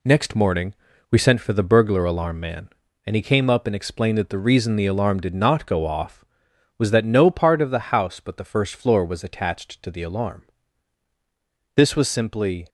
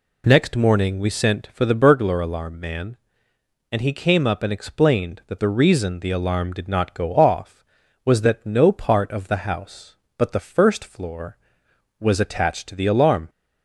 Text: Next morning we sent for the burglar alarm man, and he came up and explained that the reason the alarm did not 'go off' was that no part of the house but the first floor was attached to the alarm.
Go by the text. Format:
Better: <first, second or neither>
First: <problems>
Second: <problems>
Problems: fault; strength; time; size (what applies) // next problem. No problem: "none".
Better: second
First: pauses between "morning" and "we"; slight; at 0.7 s; 0.36 s long // goes on to say "This was simply"; noticeable; from 11.7 s on; 0.94 s long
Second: none